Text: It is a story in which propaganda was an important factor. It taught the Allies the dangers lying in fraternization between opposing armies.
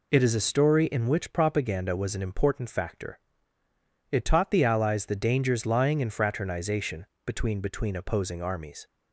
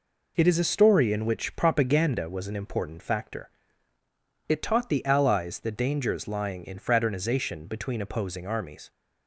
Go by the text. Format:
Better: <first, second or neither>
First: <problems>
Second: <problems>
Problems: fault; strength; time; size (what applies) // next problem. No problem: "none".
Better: second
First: pauses between "fraternization" and "between"; slight; at 7.0 s; 0.20 s long // says "between" twice; at 7.5 s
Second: none